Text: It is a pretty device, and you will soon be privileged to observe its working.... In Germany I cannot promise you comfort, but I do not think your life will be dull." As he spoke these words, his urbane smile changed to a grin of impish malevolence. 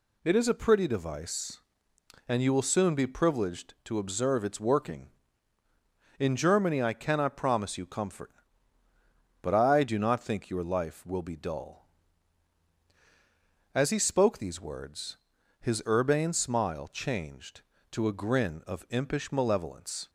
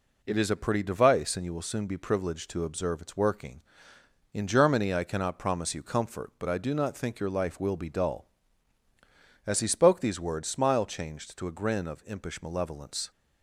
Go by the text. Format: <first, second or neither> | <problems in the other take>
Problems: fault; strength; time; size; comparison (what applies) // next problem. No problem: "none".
first | skips "his urbane"; at 10.4 s